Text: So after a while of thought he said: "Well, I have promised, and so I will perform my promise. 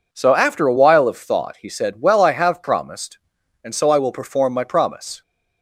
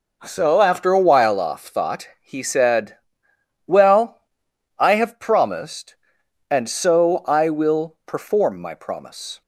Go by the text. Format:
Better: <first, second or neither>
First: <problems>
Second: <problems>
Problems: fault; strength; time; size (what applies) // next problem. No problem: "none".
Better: first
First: none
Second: says "off" for "of"; at 1.3 s